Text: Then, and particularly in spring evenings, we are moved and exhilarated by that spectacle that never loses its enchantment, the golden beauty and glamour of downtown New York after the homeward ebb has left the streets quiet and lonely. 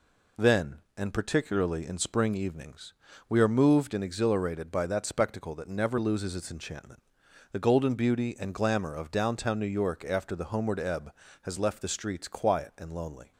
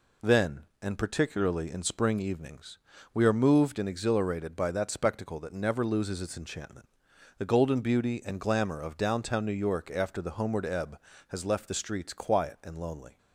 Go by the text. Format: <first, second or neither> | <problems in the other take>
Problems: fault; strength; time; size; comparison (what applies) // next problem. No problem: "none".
neither | none